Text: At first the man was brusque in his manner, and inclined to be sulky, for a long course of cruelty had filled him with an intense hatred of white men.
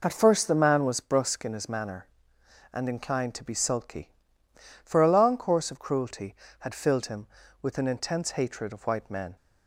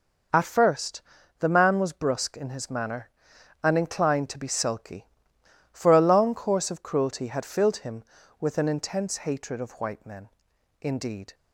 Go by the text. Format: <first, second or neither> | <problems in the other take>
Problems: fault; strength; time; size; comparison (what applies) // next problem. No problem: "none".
first | pauses between "first" and "the"; at 1.0 s; 0.38 s long // goes on to say "Indeed"; from 10.8 s on; 0.52 s long